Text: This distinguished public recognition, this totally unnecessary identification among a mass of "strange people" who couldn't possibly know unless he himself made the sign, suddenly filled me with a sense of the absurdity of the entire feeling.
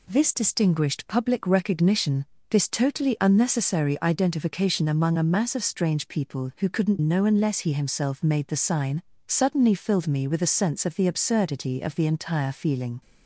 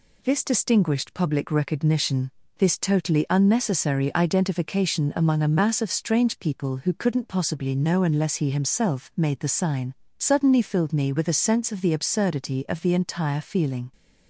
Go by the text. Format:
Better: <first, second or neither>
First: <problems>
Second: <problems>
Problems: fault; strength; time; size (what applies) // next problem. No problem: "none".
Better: second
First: skips "possibly"; at 6.9 s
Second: none